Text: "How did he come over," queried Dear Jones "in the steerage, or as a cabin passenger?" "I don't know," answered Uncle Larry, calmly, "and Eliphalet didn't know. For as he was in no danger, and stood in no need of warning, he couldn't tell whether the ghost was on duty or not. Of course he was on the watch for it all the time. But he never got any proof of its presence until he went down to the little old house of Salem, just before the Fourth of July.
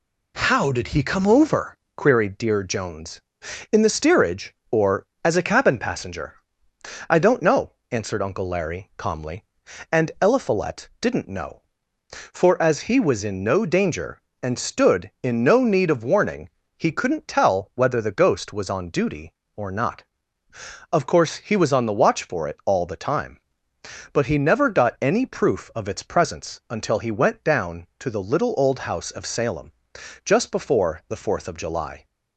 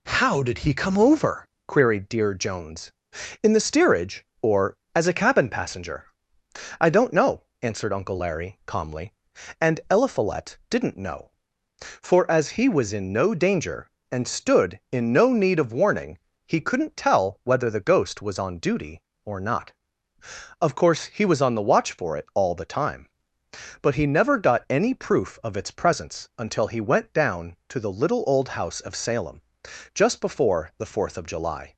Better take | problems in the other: neither | none

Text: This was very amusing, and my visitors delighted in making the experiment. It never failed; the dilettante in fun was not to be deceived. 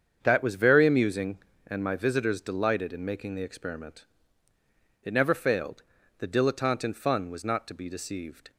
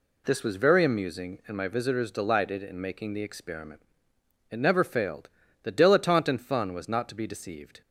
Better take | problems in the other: second | starts louder than the rest; strong; until 1.2 s; 7.5 dB // says "That" for "This"; at 0.2 s

